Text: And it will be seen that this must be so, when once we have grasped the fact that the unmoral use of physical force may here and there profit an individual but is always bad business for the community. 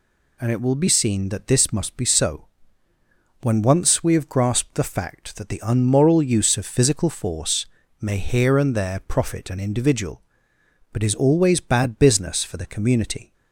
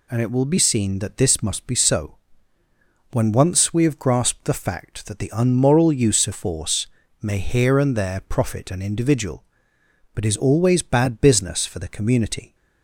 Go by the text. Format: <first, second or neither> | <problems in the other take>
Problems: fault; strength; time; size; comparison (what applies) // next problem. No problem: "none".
first | skips "physical"; at 6.3 s // pauses between "force" and "may"; slight; at 6.8 s; 0.34 s long; slight in the first